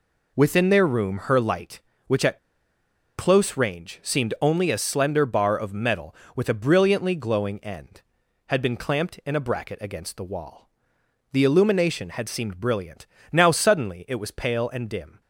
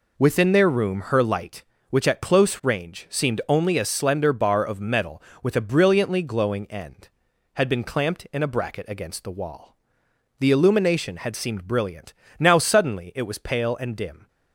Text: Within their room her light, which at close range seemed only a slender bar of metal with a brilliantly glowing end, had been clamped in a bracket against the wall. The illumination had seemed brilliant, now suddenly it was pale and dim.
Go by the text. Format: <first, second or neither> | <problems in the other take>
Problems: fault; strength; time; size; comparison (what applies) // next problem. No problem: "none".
second | pauses between "at" and "close"; noticeable; at 2.3 s; 0.79 s long